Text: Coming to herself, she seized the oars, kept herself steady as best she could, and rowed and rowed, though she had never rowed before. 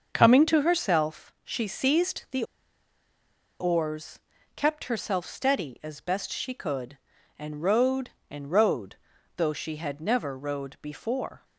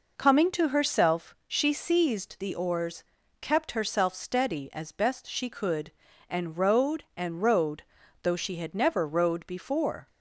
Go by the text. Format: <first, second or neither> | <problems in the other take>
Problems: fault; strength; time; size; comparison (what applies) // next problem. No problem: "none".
second | starts louder than the rest; until 1.1 s; 6.5 dB // pauses between "the" and "oars"; at 2.4 s; 1.1 s long